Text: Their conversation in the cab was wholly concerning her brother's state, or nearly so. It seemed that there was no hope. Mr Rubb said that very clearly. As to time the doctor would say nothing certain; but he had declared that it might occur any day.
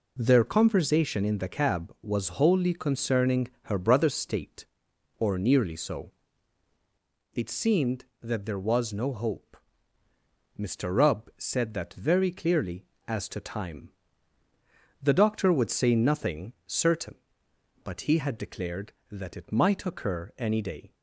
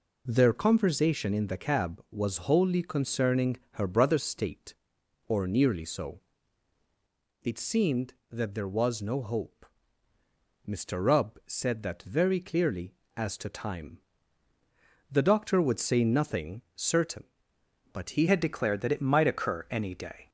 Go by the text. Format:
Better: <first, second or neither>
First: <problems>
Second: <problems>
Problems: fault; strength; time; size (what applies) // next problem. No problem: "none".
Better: first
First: pauses between "concerning" and "her"; slight; at 3.4 s; 0.16 s long // pauses between "time" and "the"; at 13.9 s; 1.1 s long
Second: pauses between "concerning" and "her"; slight; at 3.5 s; 0.16 s long // pauses between "time" and "the"; at 14.0 s; 1.1 s long // changes voice at "had"; from 18.2 s on; 2.0 s long